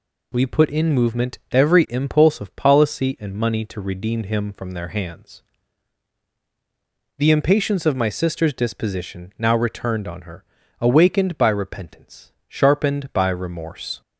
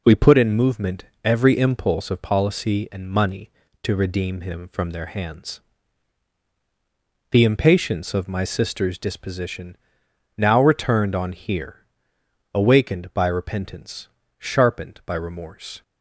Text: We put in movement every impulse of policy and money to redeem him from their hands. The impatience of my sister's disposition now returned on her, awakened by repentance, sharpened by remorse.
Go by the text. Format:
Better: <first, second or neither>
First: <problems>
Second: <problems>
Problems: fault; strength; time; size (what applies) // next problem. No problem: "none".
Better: first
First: none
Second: pauses between "movement" and "every"; slight; at 1.0 s; 0.18 s long // pauses between "disposition" and "now"; noticeable; at 9.7 s; 0.60 s long // says "here" for "her"; at 11.3 s